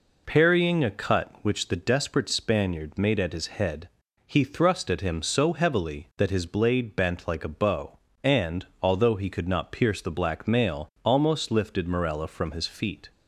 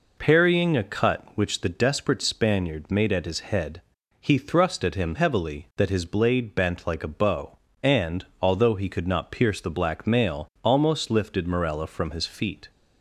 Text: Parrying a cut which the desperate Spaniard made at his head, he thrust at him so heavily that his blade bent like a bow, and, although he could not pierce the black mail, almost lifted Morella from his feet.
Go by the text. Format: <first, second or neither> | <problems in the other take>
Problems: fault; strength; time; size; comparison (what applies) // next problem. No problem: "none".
first | skips "so"; at 5.1 s